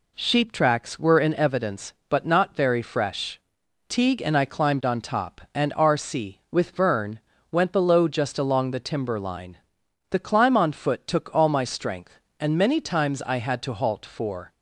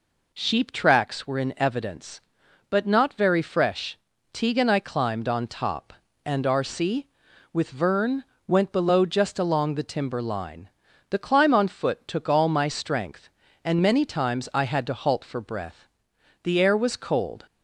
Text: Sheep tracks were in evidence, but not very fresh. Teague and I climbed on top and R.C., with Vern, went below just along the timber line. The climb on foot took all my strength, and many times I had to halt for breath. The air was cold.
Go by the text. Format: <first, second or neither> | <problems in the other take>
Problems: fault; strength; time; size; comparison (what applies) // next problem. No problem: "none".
second | stops before "breath The air was cold"; at 14.5 s